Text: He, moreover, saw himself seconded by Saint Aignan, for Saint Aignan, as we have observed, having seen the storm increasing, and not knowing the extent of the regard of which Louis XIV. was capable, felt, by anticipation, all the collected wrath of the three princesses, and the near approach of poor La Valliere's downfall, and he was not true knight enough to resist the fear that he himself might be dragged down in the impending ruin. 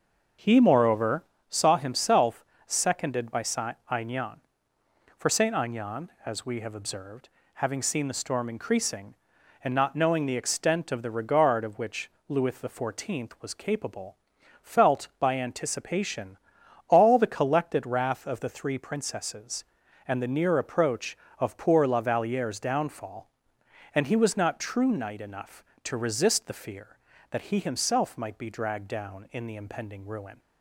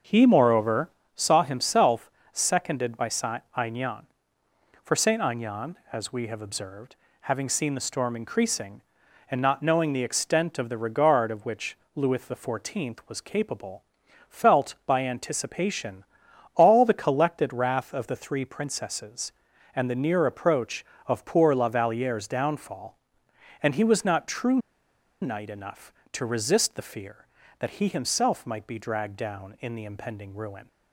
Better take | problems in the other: first | starts louder than the rest; until 1.3 s; 6 dB; also in the first // pauses between "himself" and "seconded"; slight; at 2.1 s; 0.20 s long; slight in the first // pauses between "Saint" and "Aignan"; slight; at 3.4 s; 0.16 s long; slight in the first // pauses between "which" and "Louis"; slight; at 11.7 s; 0.16 s long; slight in the first // pauses between "true" and "knight"; noticeable; at 24.5 s; 0.63 s long

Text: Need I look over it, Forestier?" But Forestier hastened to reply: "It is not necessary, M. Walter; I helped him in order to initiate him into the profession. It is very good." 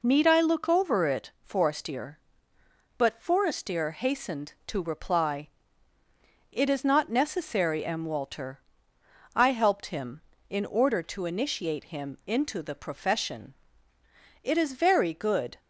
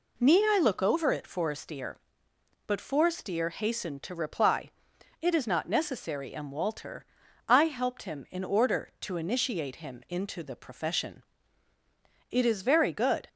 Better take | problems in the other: neither | none

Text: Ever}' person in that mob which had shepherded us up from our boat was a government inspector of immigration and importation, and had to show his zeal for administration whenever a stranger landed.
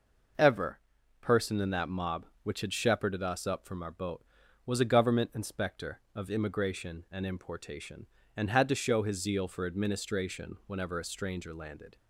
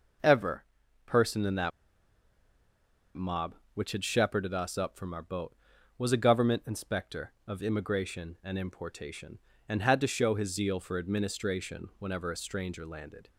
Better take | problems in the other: first | pauses between "that" and "mob"; strong; at 1.7 s; 1.4 s long

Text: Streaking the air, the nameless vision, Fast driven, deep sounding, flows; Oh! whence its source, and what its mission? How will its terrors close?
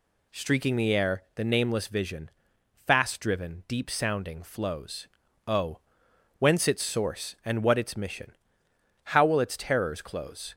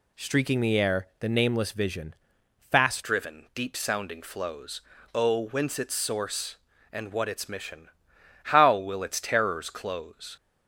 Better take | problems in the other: first | changes voice at "driven"; from 3.0 s on; 7.3 s long

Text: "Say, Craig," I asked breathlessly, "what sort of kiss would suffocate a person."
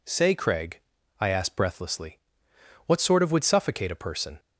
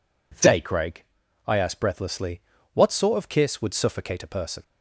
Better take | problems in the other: second | skips "kiss"; at 3.3 s

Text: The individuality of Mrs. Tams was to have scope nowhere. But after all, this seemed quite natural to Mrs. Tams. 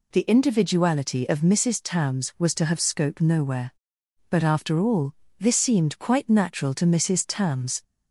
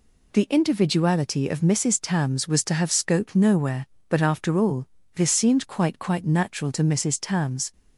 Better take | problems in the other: first | says "quite" twice; at 5.9 s

